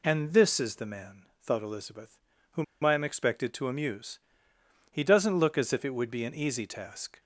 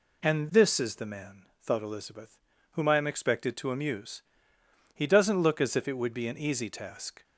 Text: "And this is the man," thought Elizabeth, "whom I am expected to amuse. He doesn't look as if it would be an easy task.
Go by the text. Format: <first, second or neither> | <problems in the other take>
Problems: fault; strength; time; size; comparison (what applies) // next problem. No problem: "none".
second | pauses between "whom" and "I"; slight; at 2.6 s; 0.19 s long